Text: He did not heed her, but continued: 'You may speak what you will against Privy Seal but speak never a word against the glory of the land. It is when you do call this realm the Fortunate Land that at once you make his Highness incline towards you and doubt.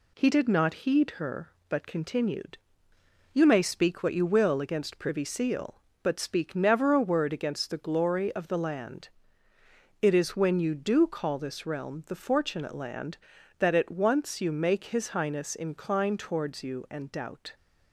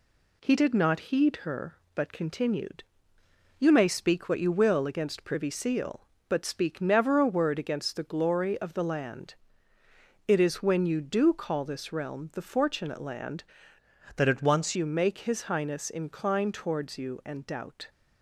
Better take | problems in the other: first | changes voice from "that" to "once"; from 14.1 to 14.7 s; 0.6 s long

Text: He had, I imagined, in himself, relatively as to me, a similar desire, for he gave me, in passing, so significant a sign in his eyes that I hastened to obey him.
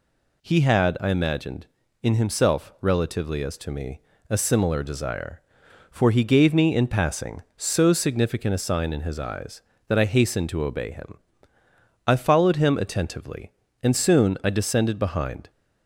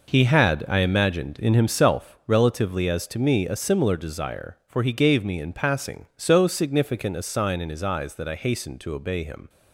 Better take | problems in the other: second | goes on to say "I followed him attentively and soon I descended behind"; strong; from 12.0 s on; 3.4 s long

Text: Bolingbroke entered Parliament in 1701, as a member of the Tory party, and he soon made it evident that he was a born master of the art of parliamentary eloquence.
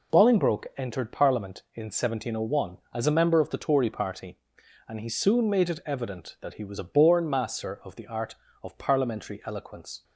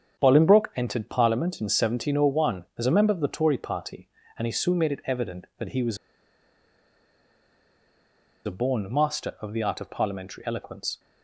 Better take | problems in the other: first | starts louder than the rest; strong; until 1.2 s; 7.5 dB // pauses between "was" and "a"; strong; at 5.9 s; 2.4 s long

